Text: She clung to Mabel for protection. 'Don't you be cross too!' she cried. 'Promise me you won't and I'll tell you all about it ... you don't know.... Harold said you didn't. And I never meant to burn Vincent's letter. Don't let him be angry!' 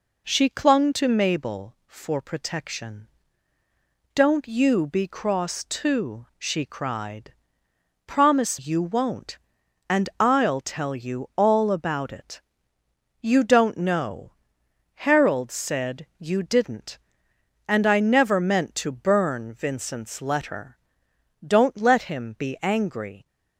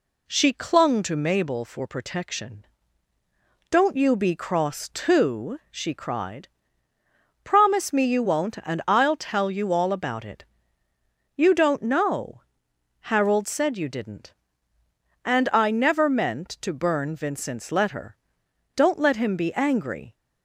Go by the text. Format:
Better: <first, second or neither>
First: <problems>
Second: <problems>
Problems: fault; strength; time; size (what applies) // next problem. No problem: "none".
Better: second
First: skips "me"; at 8.5 s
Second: none